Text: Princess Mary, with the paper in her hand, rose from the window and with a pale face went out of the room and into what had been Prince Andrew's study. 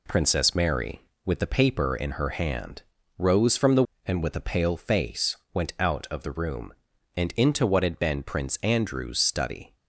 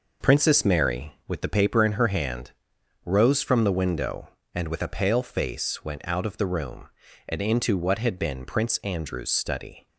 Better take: second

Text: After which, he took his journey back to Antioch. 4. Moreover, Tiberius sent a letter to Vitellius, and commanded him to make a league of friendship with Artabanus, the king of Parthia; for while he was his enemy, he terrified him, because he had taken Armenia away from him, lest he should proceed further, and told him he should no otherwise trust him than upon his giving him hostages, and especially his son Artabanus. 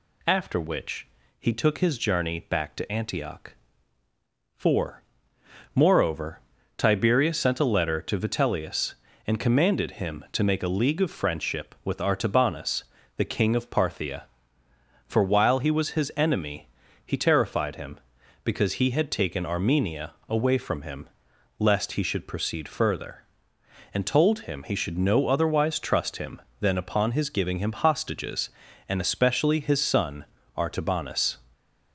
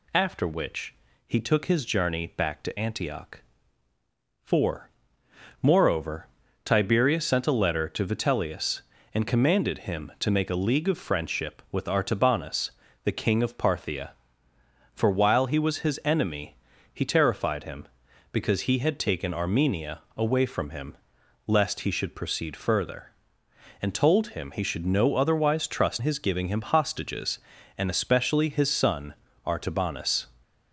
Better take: first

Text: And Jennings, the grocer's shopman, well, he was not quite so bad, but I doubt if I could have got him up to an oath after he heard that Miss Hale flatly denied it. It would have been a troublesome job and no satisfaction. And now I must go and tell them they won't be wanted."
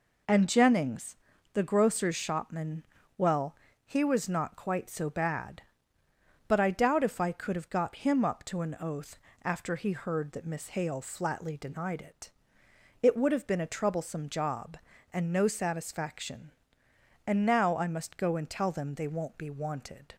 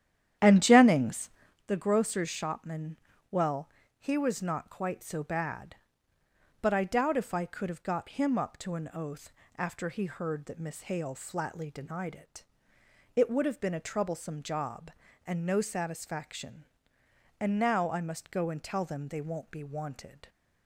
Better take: first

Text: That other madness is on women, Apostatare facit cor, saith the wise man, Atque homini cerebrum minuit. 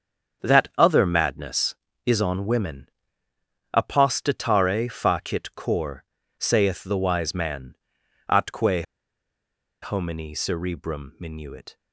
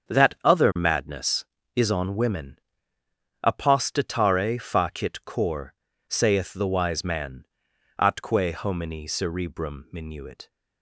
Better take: second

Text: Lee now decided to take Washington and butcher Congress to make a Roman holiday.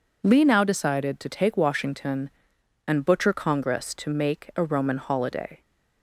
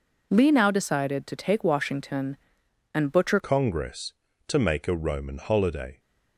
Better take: first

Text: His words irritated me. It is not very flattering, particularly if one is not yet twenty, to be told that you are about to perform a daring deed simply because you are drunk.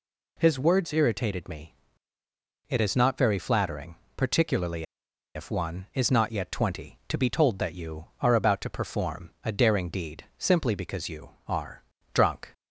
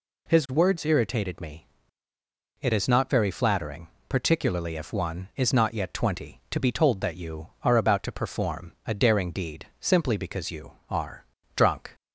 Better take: second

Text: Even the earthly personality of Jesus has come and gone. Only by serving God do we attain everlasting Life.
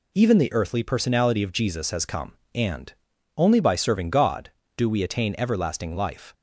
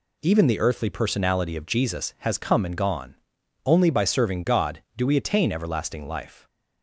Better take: second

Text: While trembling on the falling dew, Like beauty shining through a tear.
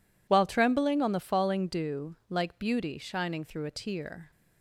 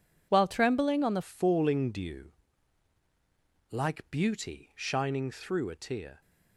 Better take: first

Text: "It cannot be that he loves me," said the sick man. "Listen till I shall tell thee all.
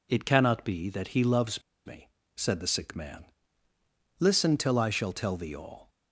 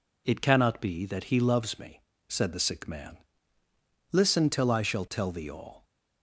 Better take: second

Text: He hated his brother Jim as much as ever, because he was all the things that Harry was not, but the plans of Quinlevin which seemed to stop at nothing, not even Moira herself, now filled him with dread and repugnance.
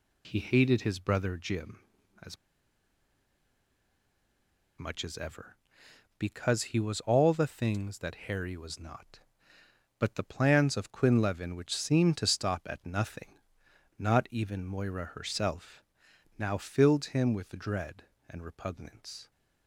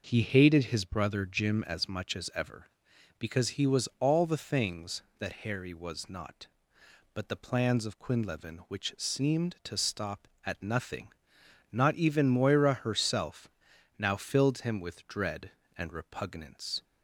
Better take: second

